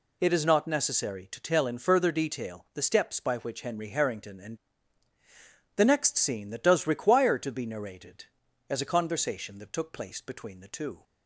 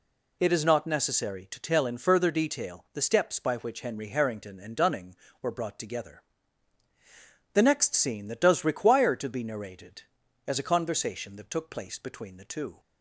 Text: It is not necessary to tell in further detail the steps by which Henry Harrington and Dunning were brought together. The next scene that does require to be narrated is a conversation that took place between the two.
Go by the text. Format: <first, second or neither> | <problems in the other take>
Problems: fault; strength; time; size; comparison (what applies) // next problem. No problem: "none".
second | skips "Dunning were brought together"; at 5.1 s